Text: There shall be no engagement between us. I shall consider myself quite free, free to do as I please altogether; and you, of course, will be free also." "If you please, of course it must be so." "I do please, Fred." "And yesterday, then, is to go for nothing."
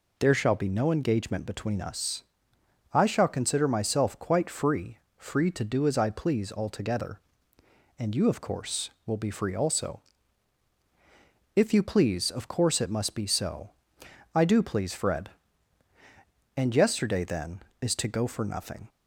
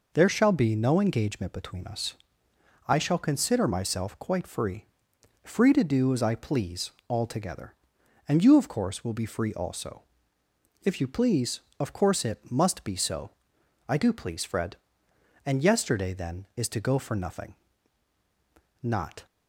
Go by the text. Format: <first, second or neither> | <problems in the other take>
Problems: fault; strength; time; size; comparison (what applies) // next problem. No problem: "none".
first | pauses between "please" and "altogether"; slight; at 6.8 s; 0.18 s long // goes on to say "Not"; slight; from 18.8 s on; 0.44 s long